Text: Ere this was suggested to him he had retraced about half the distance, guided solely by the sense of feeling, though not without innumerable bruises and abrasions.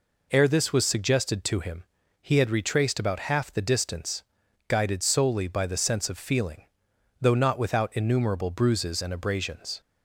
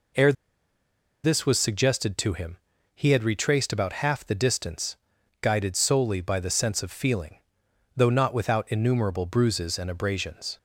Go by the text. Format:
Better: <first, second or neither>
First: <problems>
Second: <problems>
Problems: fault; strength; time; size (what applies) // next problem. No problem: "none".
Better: first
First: pauses between "him" and "he"; at 1.8 s; 0.38 s long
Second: pauses between "Ere" and "this"; noticeable; at 0.3 s; 0.91 s long // pauses between "him" and "he"; at 2.5 s; 0.38 s long